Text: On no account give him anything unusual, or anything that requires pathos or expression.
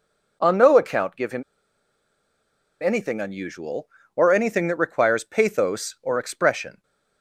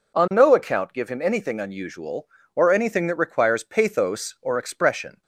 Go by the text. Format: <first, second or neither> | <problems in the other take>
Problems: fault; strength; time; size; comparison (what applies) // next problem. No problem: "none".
second | pauses between "him" and "anything"; strong; at 1.4 s; 1.3 s long